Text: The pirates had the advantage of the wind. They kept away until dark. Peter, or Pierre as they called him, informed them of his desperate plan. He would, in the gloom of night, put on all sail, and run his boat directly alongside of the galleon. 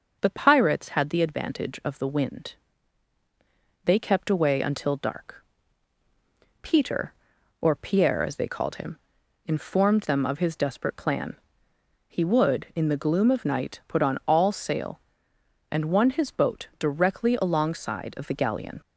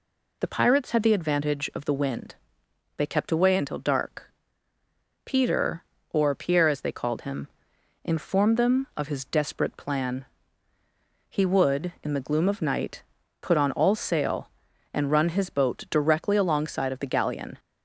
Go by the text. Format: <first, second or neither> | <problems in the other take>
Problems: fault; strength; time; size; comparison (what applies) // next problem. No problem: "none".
second | says "won" for "run"; at 15.8 s